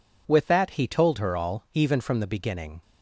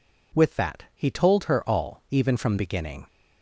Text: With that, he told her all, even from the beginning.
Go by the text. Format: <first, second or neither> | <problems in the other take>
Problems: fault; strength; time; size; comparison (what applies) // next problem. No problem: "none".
first | skips "the"; at 2.5 s